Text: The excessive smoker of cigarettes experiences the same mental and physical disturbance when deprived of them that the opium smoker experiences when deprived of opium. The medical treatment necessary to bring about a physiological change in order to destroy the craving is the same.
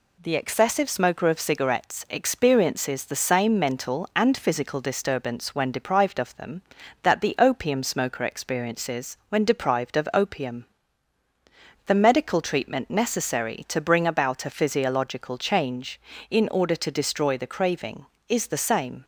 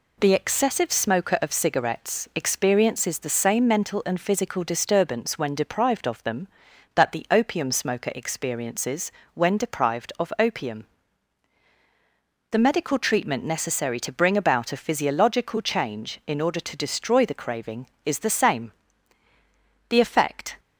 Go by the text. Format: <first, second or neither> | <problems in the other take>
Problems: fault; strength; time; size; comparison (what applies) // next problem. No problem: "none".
first | pauses between "experiences" and "when"; slight; at 9.1 s; 0.22 s long // goes on to say "The effect"; noticeable; from 19.8 s on; 0.72 s long